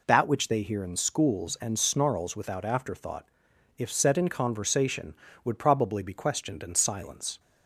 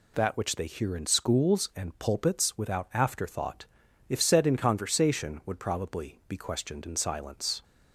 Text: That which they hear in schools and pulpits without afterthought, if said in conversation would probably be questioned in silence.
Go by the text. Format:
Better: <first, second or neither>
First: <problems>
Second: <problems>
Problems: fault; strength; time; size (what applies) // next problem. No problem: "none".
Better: second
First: says "snarls" for "pulpits"; at 1.7 s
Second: none